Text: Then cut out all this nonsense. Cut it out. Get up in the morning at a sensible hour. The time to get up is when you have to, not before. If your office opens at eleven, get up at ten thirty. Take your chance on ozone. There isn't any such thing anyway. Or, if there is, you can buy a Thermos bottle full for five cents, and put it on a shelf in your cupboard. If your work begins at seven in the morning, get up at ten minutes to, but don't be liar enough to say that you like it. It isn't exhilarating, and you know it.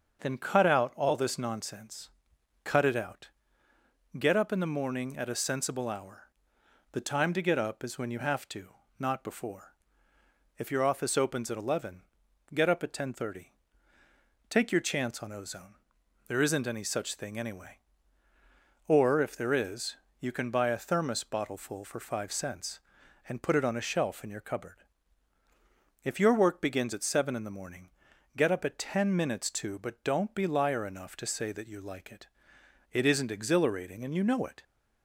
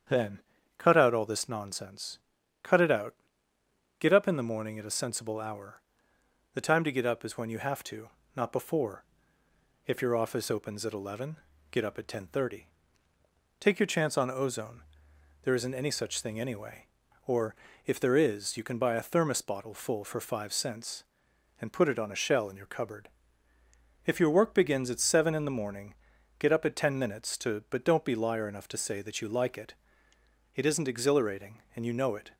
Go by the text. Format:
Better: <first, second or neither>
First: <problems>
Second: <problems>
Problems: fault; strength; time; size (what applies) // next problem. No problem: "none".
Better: first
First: starts louder than the rest; until 1.2 s; 6.5 dB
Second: starts louder than the rest; strong; until 1.4 s; 8 dB // pauses between "Then" and "cut"; at 0.3 s; 0.38 s long // says "shell" for "shelf"; at 22.1 s